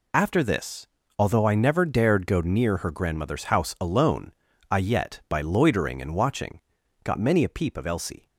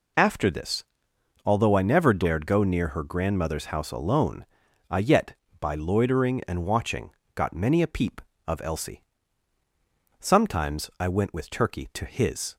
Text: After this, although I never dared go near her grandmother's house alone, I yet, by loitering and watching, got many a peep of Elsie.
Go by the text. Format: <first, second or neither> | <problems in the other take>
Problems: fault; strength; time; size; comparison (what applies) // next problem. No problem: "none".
first | goes on to say "Sometimes I went with Turkey to his"; strong; from 10.1 s on; 2.3 s long